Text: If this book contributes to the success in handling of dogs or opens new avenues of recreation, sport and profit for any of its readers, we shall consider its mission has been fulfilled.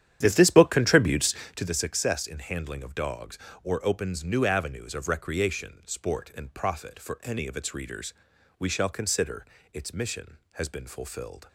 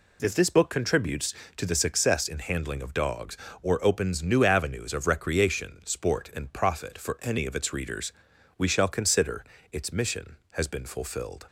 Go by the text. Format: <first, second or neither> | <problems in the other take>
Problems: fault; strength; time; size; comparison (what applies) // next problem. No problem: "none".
second | starts louder than the rest; strong; until 1.7 s; 10 dB // pauses between "consider" and "its"; slight; at 9.4 s; 0.26 s long; slight in the second